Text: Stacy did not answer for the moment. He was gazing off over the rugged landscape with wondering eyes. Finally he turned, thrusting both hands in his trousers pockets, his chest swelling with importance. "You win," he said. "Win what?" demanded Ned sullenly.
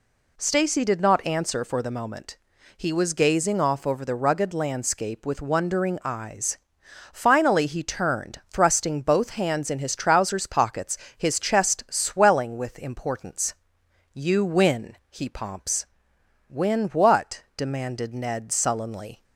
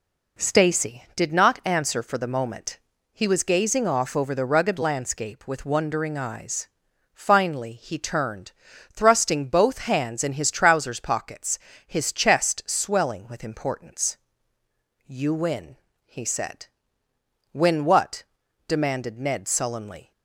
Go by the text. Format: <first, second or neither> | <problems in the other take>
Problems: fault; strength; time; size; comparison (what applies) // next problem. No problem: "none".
second | says "pomps" for "said"; at 15.2 s